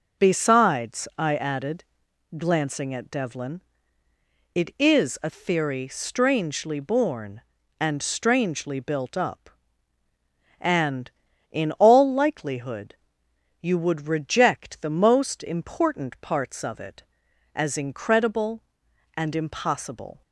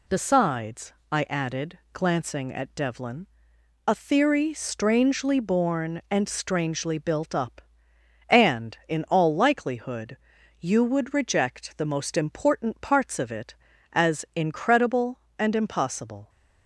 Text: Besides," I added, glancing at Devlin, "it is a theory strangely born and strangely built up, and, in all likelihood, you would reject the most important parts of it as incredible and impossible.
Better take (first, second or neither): first